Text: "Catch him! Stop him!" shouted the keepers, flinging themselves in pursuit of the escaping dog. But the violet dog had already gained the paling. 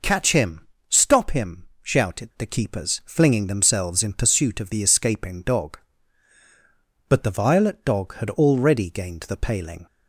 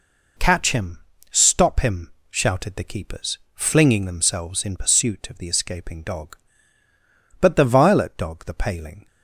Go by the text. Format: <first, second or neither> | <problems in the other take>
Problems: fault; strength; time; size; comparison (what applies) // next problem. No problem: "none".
first | skips "had already gained"; at 8.4 s